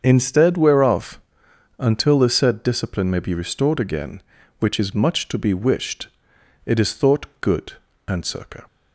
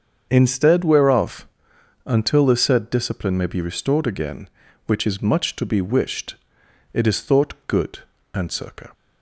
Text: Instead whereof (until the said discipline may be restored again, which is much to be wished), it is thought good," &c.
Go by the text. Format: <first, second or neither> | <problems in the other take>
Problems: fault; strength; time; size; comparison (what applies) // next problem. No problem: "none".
neither | starts louder than the rest; the same in both